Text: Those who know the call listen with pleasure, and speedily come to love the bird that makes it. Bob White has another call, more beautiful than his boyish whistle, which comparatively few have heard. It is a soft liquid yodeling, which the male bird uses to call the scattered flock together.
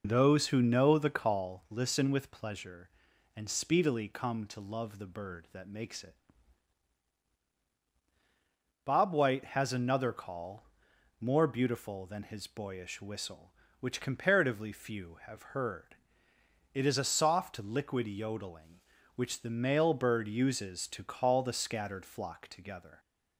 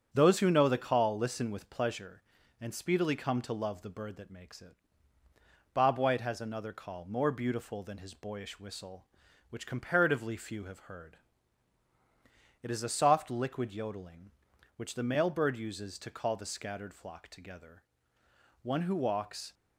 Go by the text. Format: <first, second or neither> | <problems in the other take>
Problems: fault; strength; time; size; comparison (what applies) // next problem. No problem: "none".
first | starts louder than the rest; strong; until 1.1 s; 7.5 dB // goes on to say "One who walks"; noticeable; from 18.6 s on; 0.90 s long